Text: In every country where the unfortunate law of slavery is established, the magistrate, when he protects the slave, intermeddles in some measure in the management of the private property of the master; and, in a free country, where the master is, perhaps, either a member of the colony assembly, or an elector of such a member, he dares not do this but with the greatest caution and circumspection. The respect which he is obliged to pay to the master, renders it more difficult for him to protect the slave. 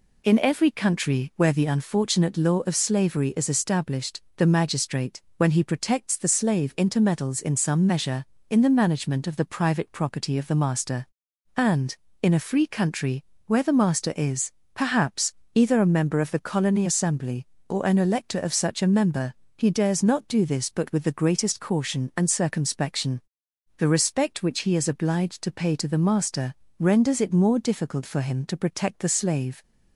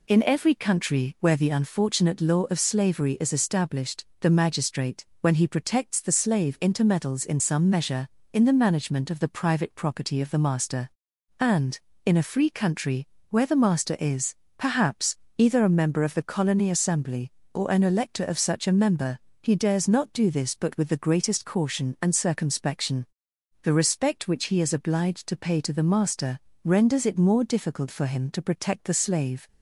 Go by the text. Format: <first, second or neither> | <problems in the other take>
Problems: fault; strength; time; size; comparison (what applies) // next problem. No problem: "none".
neither | none